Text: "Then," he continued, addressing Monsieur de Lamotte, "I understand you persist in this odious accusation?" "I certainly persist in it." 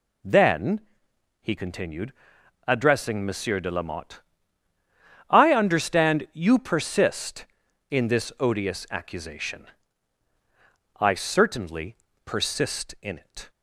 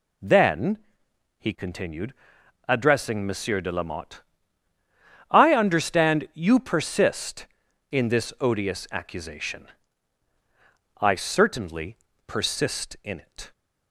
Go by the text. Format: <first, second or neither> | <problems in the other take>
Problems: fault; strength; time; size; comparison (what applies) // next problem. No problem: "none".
neither | pauses between "certainly" and "persist"; slight; the same in both